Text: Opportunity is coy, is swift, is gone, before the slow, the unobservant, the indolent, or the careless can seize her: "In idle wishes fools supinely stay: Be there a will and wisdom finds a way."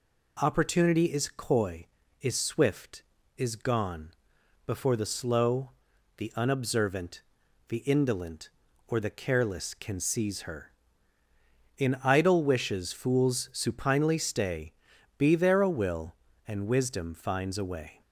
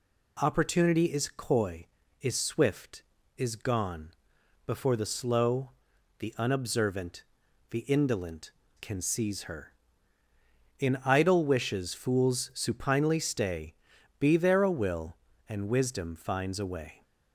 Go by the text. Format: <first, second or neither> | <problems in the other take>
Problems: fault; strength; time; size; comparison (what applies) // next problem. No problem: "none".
first | skips "or the careless"; at 8.6 s